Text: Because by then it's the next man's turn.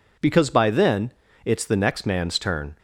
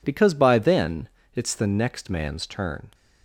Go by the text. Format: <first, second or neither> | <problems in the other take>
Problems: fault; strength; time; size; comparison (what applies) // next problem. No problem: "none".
neither | pauses between "then" and "it's"; slight; the same in both